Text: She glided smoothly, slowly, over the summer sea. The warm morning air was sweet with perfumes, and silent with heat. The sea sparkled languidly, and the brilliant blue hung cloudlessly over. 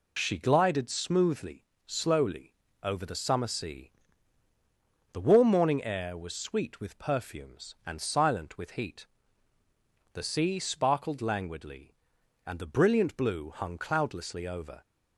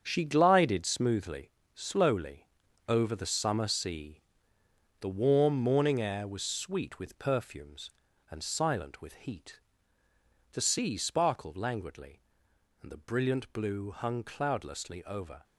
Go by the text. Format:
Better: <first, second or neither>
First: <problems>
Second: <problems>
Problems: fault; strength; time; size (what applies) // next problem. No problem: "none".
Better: first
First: none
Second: gets quieter; strong; throughout; 9.5 dB